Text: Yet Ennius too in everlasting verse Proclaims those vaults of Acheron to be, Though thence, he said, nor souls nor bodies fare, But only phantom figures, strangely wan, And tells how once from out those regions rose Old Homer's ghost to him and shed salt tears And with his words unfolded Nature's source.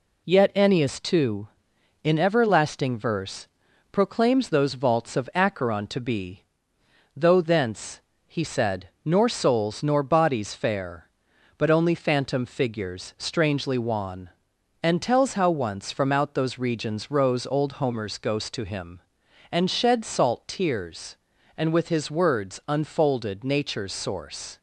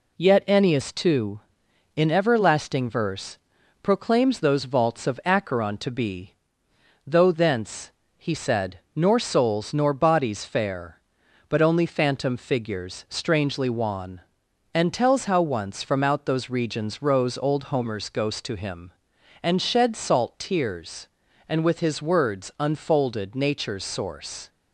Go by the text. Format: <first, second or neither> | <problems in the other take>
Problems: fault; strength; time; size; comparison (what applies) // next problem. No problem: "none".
neither | pauses between "verse" and "Proclaims"; noticeable; the same in both